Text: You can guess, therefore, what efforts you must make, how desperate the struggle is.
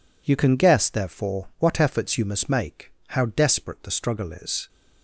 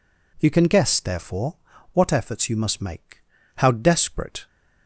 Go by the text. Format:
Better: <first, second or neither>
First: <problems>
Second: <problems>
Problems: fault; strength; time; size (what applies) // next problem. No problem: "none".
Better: first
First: none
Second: stops before "the struggle is"; at 4.4 s